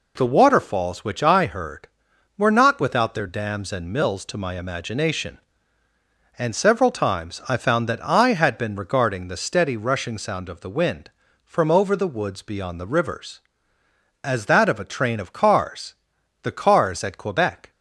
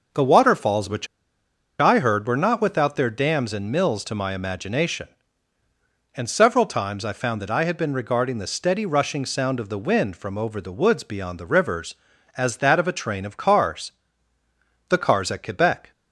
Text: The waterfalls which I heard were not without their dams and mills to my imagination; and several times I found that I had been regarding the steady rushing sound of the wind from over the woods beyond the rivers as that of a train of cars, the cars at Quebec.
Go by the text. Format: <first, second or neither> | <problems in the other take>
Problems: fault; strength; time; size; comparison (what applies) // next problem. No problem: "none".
first | pauses between "which" and "I"; noticeable; at 1.0 s; 0.72 s long